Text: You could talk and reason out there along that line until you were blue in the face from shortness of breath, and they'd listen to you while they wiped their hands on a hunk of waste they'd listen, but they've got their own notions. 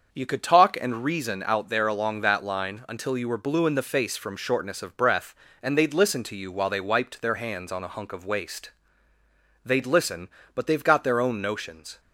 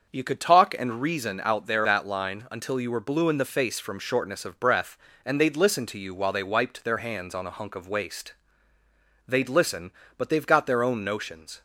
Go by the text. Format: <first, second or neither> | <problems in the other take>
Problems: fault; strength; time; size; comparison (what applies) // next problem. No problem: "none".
first | starts louder than the rest; until 1.1 s; 6.5 dB; also in the first // skips "along"; at 1.8 s // pauses between "waste" and "they'd"; noticeable; at 8.3 s; 0.92 s long; noticeable in the first